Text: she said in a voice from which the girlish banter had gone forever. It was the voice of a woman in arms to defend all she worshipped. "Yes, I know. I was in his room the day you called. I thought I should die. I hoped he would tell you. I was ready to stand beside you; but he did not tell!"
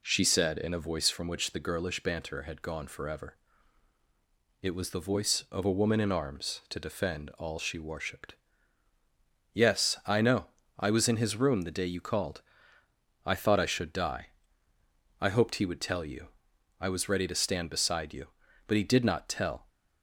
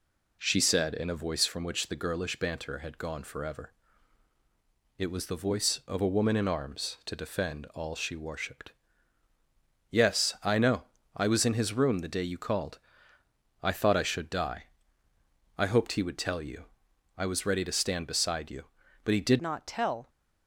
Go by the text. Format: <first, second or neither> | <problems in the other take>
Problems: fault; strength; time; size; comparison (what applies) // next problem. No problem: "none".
first | changes voice at "not"; from 19.4 s on; 0.6 s long